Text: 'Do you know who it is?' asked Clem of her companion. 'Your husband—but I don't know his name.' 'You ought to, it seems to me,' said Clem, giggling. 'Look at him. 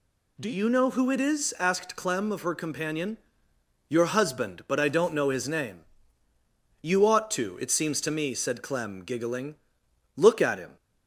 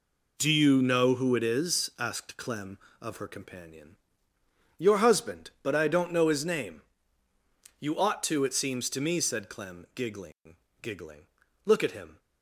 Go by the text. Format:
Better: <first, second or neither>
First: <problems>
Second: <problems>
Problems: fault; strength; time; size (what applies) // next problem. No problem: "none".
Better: first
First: none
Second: says "giggling" twice; at 10.8 s